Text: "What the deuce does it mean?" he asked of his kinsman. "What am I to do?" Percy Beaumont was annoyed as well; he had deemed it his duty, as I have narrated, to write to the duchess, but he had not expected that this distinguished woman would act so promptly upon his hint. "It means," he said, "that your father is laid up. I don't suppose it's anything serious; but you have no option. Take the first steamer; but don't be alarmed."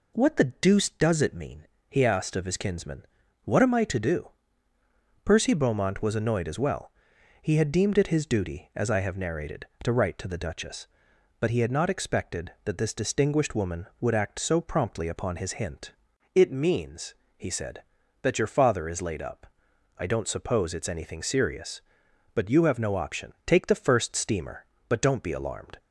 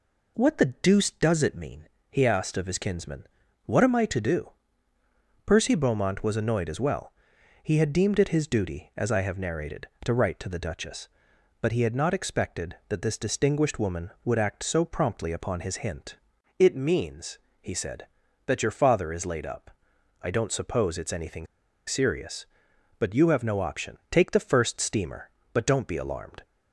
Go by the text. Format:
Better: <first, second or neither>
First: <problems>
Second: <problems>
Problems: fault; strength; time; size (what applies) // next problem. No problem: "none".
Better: first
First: none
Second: pauses between "anything" and "serious"; at 21.4 s; 0.40 s long